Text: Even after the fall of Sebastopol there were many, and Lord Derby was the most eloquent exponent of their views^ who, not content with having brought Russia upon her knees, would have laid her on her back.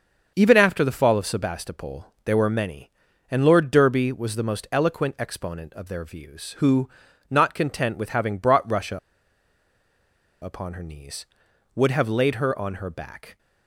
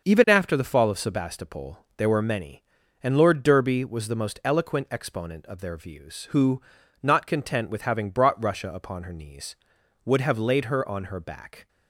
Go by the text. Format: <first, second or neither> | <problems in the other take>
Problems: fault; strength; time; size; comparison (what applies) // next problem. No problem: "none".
second | starts louder than the rest; until 1.3 s; 6.5 dB; also in the second // pauses between "Sebastopol" and "there"; slight; at 2.0 s; 0.20 s long; slight in the second // pauses between "Russia" and "upon"; strong; at 8.9 s; 1.4 s long